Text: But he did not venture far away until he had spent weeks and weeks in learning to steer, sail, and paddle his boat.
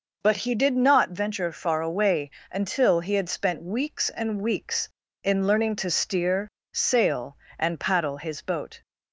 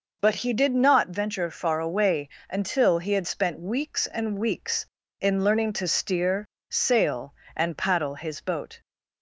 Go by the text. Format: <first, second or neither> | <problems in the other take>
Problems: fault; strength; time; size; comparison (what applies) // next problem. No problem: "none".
neither | pauses between "away" and "until"; slight; the same in both